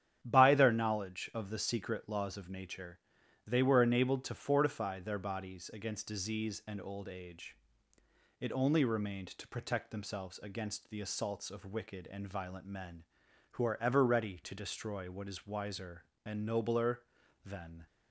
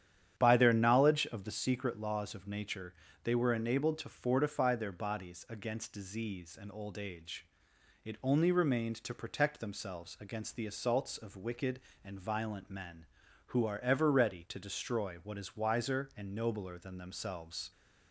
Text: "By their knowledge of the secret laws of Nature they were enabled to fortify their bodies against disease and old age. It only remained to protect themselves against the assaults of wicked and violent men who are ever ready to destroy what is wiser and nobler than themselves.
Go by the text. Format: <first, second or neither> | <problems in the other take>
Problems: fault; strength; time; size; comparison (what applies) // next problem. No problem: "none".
second | starts louder than the rest; strong; until 1.2 s; 9.5 dB; strong in the second // pauses between "Nature" and "they"; noticeable; at 2.9 s; 0.48 s long; slight in the second // stops before "themselves"; at 17.8 s